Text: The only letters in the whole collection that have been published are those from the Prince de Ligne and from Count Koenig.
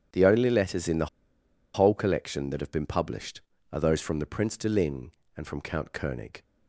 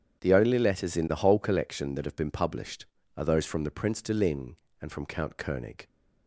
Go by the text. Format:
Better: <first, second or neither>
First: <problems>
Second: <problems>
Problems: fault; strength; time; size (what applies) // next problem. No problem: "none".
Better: second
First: starts louder than the rest; strong; until 1.8 s; 9 dB // pauses between "the" and "whole"; noticeable; at 1.0 s; 0.68 s long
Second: starts louder than the rest; strong; until 1.2 s; 8.5 dB